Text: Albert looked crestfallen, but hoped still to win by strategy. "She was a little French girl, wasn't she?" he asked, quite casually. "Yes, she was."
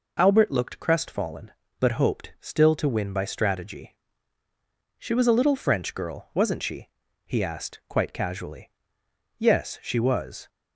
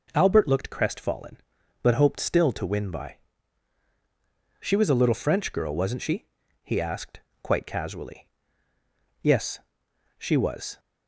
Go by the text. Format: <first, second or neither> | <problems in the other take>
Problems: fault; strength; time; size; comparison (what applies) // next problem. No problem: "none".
first | skips "strategy"; at 3.8 s